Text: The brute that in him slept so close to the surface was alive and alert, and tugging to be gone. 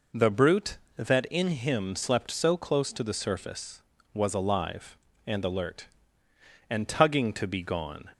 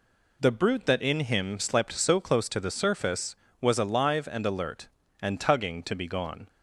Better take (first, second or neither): second